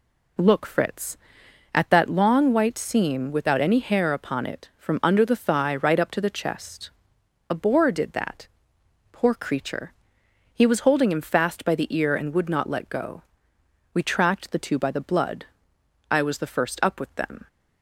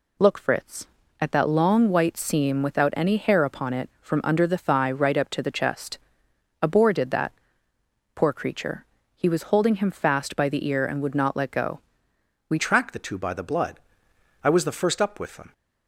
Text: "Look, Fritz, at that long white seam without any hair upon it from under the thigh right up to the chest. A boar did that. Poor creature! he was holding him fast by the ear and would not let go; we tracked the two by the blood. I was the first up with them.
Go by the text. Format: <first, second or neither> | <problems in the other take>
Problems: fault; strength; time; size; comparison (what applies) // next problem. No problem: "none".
first | changes voice at "tracked"; from 12.5 s on; 3.0 s long